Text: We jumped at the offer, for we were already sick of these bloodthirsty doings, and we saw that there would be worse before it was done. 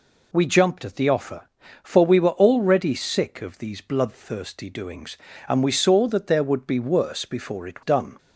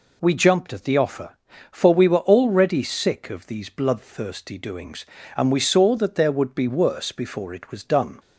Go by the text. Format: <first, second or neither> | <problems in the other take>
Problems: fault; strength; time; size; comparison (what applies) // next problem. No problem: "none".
second | skips "was"; at 7.8 s